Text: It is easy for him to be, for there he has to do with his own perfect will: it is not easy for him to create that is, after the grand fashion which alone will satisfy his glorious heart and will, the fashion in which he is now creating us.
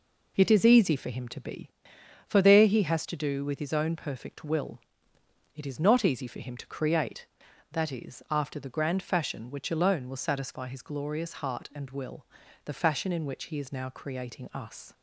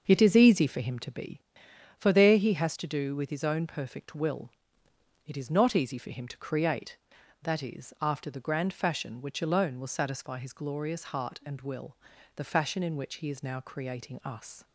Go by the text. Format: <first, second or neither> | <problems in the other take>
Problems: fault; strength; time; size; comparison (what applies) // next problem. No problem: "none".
first | starts louder than the rest; until 1.1 s; 6.5 dB